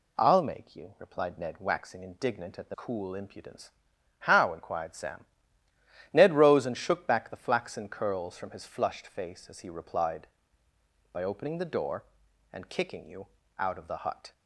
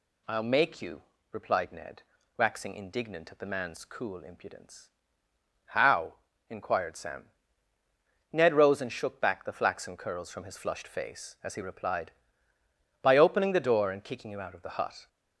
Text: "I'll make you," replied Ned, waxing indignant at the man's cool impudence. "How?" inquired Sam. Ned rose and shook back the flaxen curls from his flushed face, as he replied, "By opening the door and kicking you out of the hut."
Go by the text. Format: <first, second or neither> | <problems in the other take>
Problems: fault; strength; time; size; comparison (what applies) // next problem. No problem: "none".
second | skips "man's"; at 2.7 s // pauses between "you" and "out"; slight; at 13.2 s; 0.28 s long